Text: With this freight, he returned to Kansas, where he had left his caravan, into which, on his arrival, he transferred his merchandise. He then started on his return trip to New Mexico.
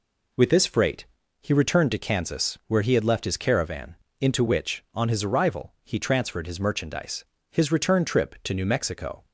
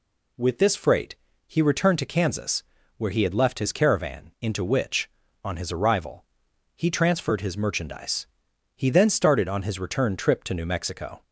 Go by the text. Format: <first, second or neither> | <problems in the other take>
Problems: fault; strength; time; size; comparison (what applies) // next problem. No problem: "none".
second | skips "He then started on"; at 7.3 s